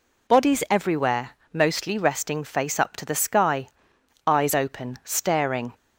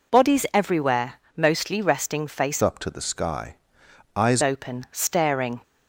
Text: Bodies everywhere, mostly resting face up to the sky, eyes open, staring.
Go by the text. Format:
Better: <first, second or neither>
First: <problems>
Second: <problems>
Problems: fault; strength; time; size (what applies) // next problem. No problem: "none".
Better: first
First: none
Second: changes voice from "up" to "eyes"; from 2.6 to 4.4 s; 1.8 s long